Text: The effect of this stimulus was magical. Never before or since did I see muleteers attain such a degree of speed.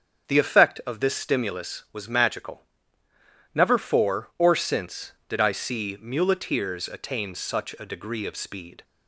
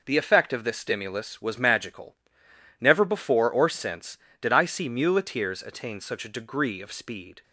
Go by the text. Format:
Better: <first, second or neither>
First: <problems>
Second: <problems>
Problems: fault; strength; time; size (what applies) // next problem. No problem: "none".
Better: second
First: starts louder than the rest; until 1.3 s; 7 dB // says "for" for "before"; at 3.7 s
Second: none